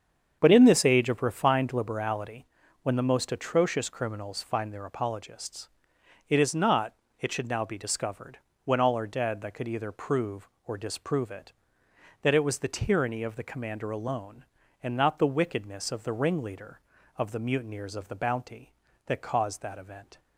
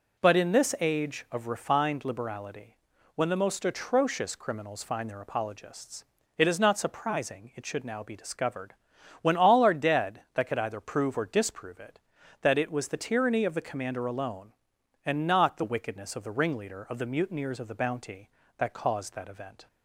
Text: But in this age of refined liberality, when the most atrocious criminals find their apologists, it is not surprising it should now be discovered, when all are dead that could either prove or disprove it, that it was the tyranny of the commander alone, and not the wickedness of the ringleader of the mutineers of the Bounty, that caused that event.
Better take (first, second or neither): second